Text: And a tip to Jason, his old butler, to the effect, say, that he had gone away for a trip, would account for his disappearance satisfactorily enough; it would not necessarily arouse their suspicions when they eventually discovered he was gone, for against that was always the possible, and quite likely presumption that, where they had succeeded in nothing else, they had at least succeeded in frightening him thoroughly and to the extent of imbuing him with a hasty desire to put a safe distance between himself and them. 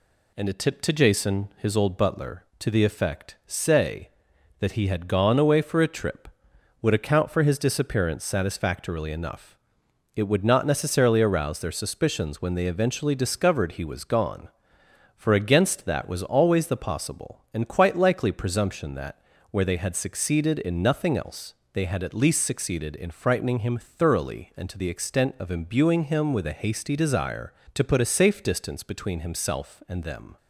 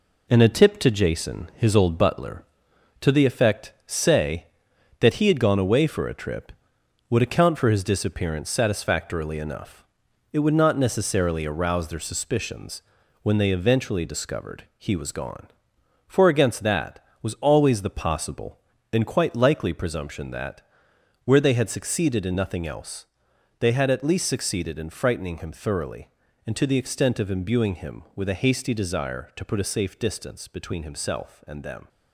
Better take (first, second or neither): first